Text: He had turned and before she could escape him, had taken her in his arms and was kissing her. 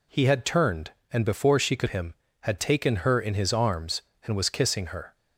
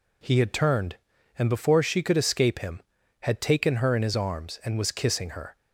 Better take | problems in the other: second | skips "escape"; at 1.8 s

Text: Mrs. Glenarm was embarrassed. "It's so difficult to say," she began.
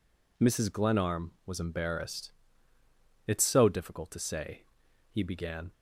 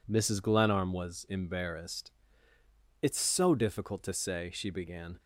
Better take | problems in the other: second | says "he" for "she"; at 5.0 s

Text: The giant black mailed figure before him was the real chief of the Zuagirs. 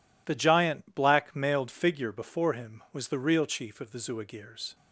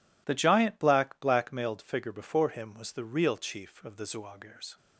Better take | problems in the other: first | says "black" twice; at 1.1 s

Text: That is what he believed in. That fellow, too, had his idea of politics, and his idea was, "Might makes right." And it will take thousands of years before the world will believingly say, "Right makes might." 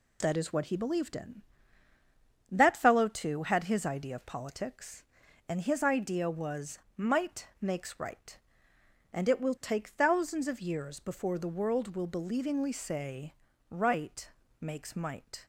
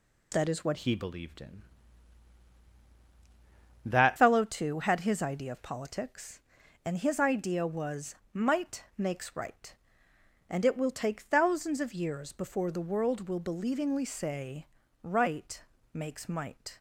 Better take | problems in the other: first | changes voice from "he" to "That"; from 0.7 to 4.1 s; 3.4 s long // pauses between "Right" and "makes"; slight; at 15.5 s; 0.34 s long; slight in the first

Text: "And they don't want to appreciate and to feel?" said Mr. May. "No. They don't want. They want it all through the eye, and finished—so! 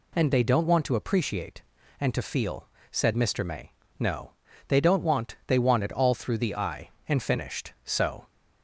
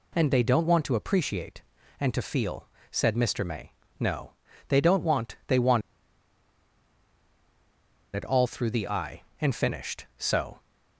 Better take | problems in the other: first | pauses between "want" and "it"; strong; at 5.8 s; 2.3 s long

